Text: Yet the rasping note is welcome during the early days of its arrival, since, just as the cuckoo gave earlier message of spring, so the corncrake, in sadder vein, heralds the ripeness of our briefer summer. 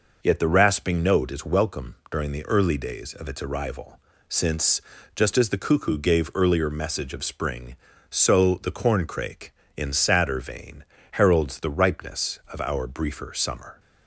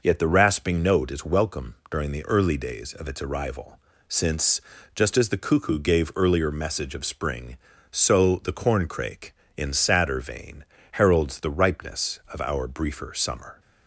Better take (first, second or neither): neither